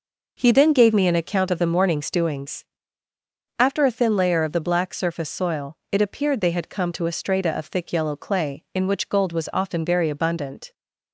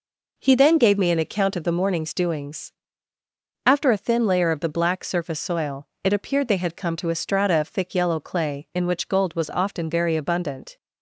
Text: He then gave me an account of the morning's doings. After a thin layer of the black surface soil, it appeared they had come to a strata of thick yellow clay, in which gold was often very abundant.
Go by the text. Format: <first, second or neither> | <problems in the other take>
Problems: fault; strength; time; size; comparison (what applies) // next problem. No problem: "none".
neither | none